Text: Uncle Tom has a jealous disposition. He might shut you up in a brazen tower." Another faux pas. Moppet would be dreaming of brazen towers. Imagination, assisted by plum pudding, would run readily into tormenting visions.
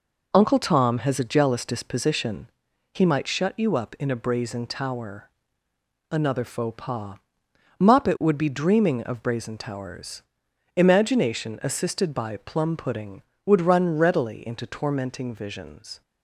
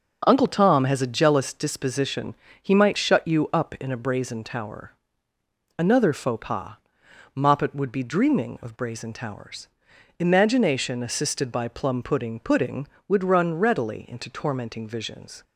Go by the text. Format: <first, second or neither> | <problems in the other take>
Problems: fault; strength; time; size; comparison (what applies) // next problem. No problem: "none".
first | starts louder than the rest; noticeable; until 1.2 s; 6 dB // says "pudding" twice; at 12.3 s